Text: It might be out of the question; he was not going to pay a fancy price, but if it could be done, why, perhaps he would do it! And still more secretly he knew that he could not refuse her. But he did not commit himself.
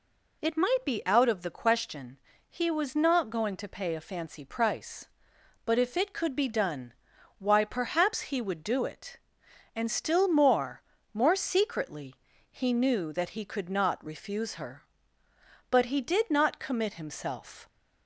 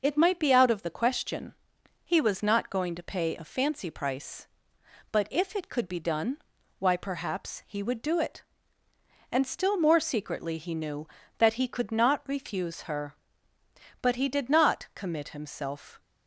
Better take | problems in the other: second | says "more" twice; at 11.1 s // pauses between "secretly" and "he"; at 12.1 s; 0.38 s long

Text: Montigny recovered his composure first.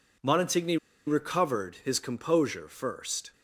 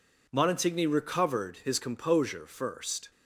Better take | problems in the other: second | pauses between "Montigny" and "recovered"; slight; at 0.7 s; 0.30 s long

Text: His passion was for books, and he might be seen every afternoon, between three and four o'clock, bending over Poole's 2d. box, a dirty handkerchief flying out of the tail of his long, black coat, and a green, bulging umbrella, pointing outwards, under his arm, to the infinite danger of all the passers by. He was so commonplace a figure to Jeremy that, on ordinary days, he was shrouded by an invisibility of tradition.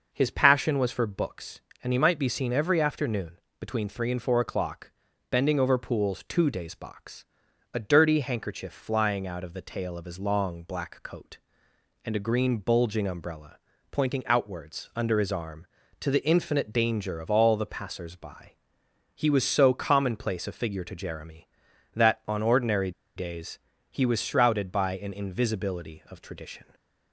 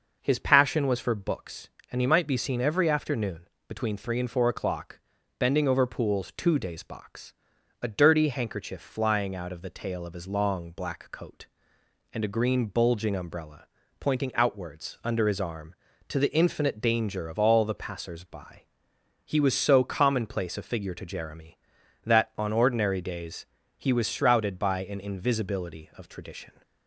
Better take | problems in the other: second | pauses between "ordinary" and "days"; slight; at 22.9 s; 0.24 s long

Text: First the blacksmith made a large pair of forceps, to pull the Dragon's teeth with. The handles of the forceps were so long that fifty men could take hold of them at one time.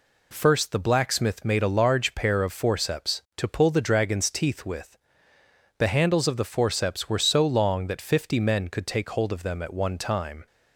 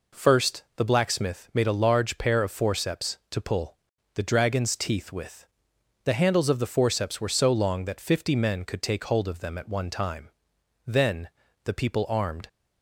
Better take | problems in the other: first | pauses between "First" and "the"; slight; at 0.6 s; 0.16 s long // pauses between "pull" and "the"; slight; at 3.7 s; 0.36 s long // goes on to say "Then the people armed"; from 10.8 s on; 1.6 s long

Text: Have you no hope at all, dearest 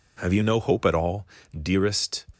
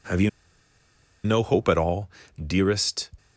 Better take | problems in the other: first | pauses between "you" and "no"; noticeable; at 0.2 s; 0.95 s long

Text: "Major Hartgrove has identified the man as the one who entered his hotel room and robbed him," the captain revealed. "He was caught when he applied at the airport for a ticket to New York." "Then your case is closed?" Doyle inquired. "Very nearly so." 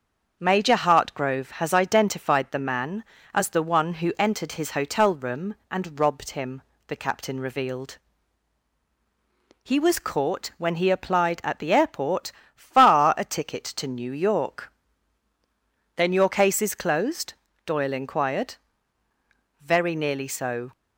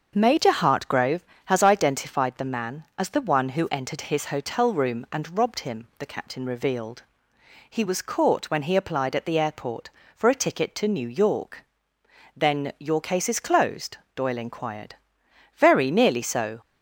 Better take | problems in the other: second | starts louder than the rest; until 1.4 s; 7 dB; also in the second // says "far" for "for"; at 12.5 s

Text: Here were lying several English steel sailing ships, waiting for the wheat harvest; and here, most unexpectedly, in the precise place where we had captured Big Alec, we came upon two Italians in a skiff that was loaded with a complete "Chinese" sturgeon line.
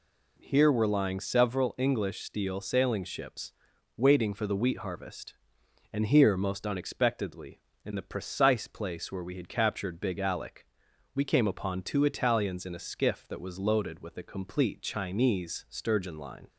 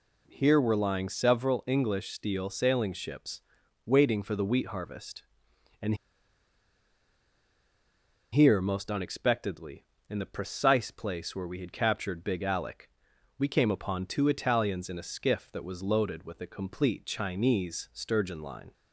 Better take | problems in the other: first | pauses between "and" and "here"; strong; at 5.9 s; 2.3 s long

